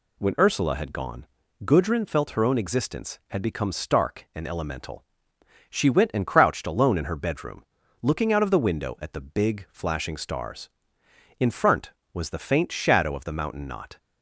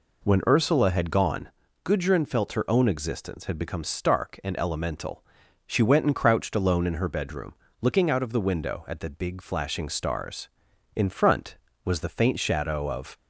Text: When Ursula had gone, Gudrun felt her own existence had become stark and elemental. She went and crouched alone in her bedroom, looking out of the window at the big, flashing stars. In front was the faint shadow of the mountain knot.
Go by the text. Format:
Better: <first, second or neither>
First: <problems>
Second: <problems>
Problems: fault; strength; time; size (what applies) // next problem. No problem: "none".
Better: first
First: none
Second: stops before "the mountain knot"; at 13.1 s